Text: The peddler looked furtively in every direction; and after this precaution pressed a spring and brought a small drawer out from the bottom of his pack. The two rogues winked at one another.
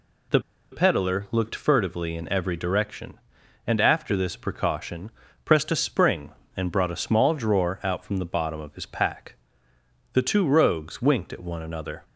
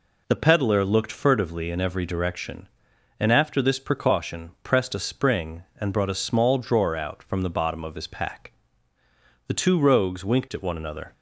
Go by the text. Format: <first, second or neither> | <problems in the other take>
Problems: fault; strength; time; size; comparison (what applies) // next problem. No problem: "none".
second | pauses between "The" and "peddler"; slight; at 0.4 s; 0.30 s long // pauses between "precaution" and "pressed"; slight; at 5.1 s; 0.34 s long